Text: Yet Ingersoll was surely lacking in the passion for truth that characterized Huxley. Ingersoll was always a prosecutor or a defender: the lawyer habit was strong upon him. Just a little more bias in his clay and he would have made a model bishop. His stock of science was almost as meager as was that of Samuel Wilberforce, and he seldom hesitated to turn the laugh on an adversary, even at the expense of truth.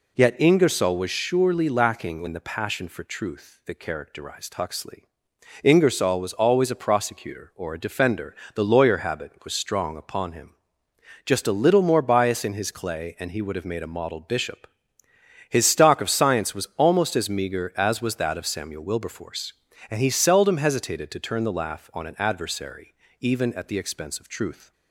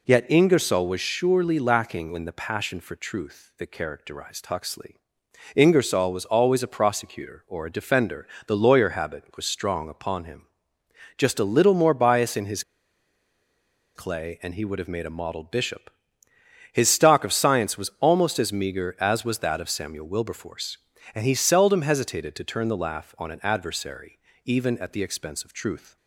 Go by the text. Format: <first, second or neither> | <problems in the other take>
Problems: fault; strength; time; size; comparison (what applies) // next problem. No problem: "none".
first | pauses between "his" and "clay"; strong; at 12.6 s; 1.3 s long